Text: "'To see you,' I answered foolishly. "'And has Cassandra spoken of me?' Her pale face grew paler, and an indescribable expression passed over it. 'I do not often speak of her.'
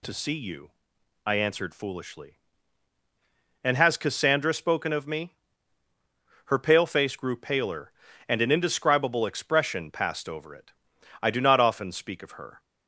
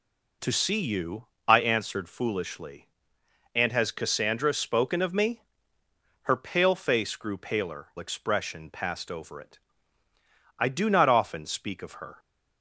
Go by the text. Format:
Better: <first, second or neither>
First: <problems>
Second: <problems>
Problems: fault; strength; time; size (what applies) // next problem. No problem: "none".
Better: first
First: none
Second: skips "and an indescribable"; at 7.9 s